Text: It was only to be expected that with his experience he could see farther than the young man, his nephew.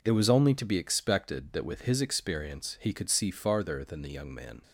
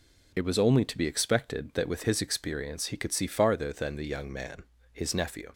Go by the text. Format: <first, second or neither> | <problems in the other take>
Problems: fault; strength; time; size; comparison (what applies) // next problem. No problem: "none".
second | stops before "his nephew"; at 4.6 s